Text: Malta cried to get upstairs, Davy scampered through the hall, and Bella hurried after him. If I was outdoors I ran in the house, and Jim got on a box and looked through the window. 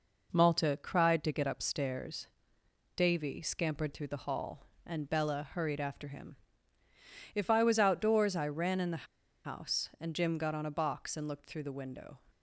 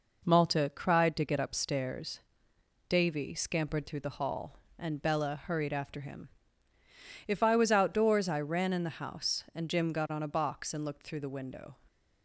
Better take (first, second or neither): second